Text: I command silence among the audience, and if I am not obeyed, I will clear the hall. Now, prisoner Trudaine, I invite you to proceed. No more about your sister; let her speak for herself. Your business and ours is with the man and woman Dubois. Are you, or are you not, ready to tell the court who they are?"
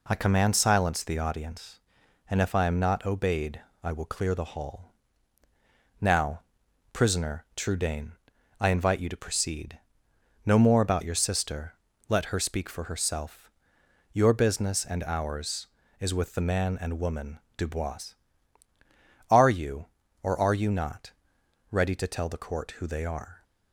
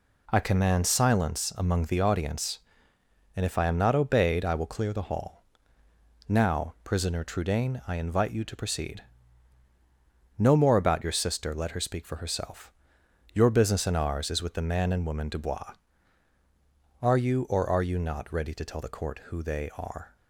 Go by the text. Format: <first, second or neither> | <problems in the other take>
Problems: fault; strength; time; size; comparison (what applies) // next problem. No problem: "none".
second | skips "among"; at 1.0 s // pauses between "woman" and "Dubois"; slight; at 17.3 s; 0.18 s long